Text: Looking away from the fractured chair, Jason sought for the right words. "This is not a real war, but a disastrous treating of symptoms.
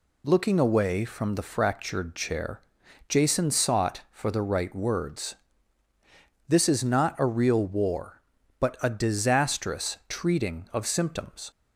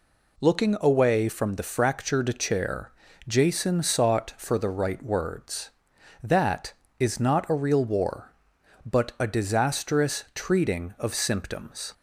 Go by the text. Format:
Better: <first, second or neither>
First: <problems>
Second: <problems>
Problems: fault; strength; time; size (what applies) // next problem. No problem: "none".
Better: first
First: none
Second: says "That" for "This"; at 6.2 s